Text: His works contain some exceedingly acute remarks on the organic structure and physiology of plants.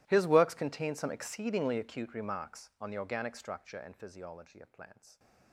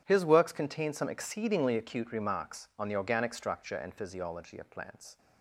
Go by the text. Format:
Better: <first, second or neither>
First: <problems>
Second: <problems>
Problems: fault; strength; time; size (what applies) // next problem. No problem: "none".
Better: second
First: gets quieter; strong; throughout; 24.5 dB // starts louder than the rest; strong; until 1.0 s; 15.5 dB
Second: starts louder than the rest; strong; until 1.0 s; 10 dB